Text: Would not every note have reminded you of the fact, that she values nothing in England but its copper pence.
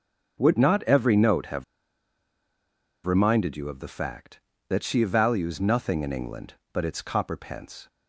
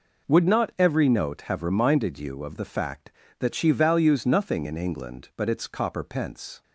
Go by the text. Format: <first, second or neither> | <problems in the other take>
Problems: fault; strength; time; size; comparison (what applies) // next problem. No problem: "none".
second | pauses between "have" and "reminded"; strong; at 1.6 s; 1.4 s long